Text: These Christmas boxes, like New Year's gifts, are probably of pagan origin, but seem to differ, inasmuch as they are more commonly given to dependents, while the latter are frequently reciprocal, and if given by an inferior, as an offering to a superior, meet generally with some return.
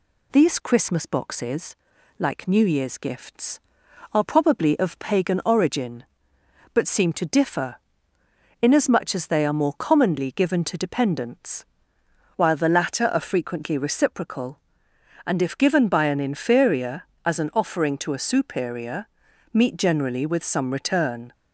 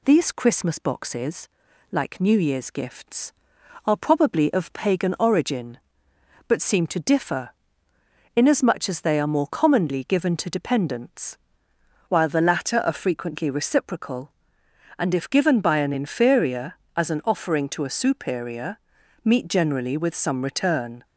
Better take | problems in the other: neither | none

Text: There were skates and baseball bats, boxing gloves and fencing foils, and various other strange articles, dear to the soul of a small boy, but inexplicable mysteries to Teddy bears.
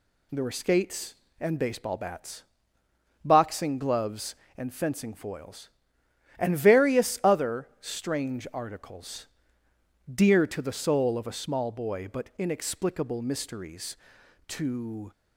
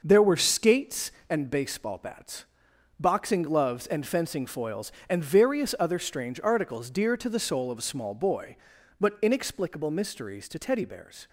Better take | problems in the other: second | stops before "Teddy bears"; at 15.1 s

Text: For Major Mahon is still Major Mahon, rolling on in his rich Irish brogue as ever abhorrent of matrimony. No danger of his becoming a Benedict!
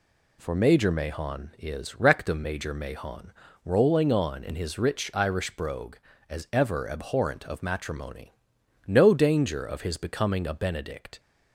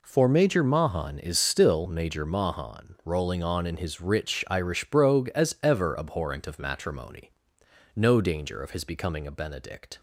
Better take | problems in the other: second | says "rectum" for "still"; at 1.9 s

